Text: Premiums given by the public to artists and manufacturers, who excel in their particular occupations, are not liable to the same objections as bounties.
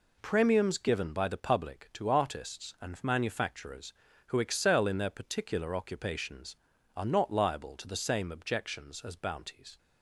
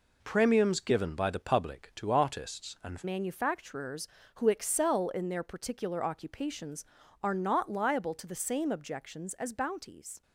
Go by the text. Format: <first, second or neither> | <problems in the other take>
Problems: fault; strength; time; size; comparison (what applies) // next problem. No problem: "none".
first | changes voice at "manufacturers"; from 3.0 s on; 7.2 s long